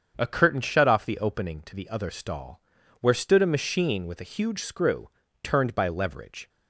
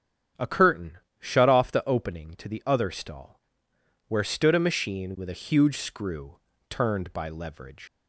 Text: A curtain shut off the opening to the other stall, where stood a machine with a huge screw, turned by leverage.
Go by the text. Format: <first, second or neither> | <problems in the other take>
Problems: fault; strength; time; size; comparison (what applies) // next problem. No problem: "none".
first | starts louder than the rest; strong; until 1.6 s; 8.5 dB; strong in the first // pauses between "curtain" and "shut"; slight; at 0.9 s; 0.24 s long // leaves "leverage" unfinished; at 7.8 s; 90 ms